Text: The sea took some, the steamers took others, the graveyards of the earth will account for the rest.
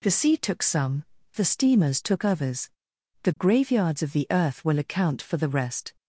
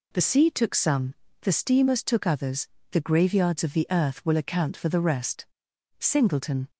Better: first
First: none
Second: goes on to say "Singleton"; noticeable; from 5.9 s on; 0.70 s long

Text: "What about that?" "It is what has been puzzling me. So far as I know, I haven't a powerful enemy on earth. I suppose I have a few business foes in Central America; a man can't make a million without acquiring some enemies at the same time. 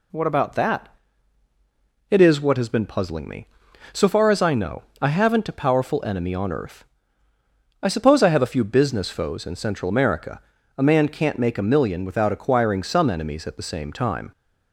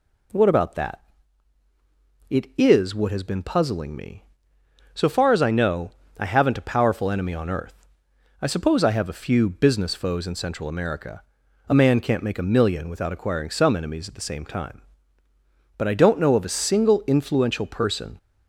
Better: first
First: none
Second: goes on to say "But I don't know of a single influential person"; strong; from 15.7 s on; 2.4 s long

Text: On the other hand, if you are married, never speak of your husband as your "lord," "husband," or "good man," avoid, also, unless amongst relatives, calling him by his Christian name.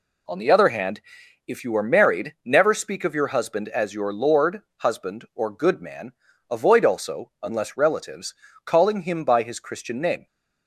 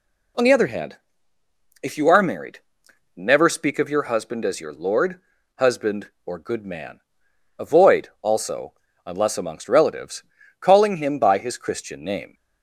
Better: second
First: skips "amongst"; at 7.7 s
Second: none

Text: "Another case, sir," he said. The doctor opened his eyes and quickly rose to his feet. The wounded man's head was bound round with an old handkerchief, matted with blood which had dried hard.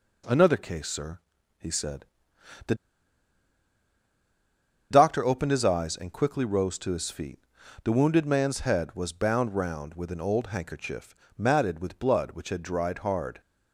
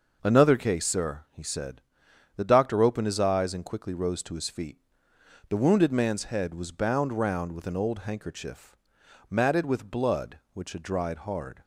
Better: second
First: pauses between "The" and "doctor"; strong; at 2.7 s; 2.1 s long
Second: none

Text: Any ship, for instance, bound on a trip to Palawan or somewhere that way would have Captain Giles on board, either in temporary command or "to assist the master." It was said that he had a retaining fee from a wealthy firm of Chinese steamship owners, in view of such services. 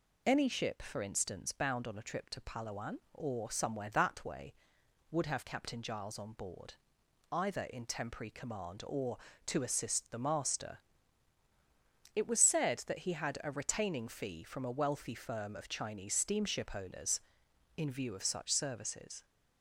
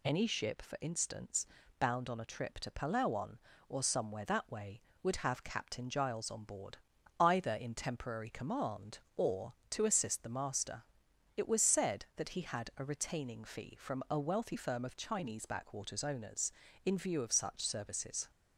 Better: first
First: none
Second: says "backwaters" for "steamship"; at 15.4 s

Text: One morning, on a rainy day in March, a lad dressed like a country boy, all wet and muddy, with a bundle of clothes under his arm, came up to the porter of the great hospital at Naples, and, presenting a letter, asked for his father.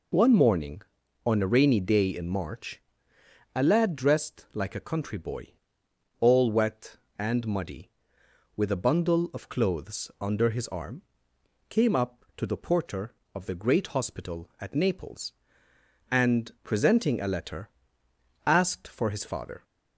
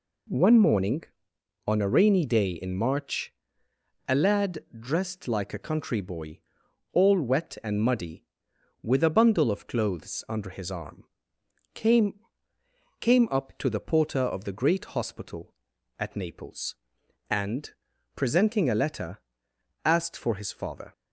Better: first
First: none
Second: pauses between "lad" and "dressed"; slight; at 4.5 s; 0.20 s long // says "came" twice; at 12.9 s

